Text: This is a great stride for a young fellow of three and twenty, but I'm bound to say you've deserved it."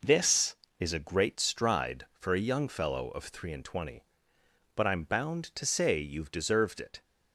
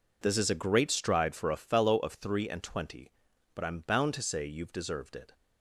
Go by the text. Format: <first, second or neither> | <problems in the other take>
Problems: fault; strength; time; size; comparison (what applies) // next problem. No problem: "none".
first | skips "young"; at 1.5 s